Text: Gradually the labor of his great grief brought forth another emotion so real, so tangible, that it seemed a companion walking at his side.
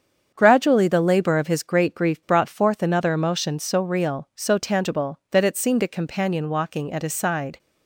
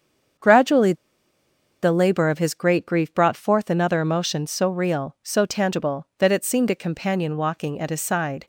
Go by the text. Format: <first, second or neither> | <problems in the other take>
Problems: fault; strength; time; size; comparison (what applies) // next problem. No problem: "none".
first | starts louder than the rest; strong; until 2.2 s; 7.5 dB; strong in the first // pauses between "Gradually" and "the"; noticeable; at 0.9 s; 0.89 s long